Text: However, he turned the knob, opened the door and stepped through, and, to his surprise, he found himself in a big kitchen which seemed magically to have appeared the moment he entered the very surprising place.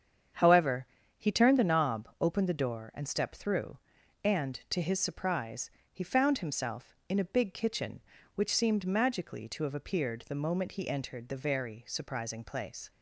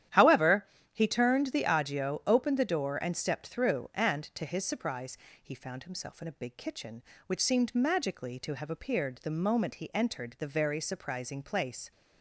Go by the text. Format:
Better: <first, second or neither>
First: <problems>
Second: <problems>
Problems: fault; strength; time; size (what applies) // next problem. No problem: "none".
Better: first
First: starts louder than the rest; strong; until 1.6 s; 8 dB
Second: starts louder than the rest; strong; until 1.3 s; 11 dB // says "agio" for "knob"; at 1.6 s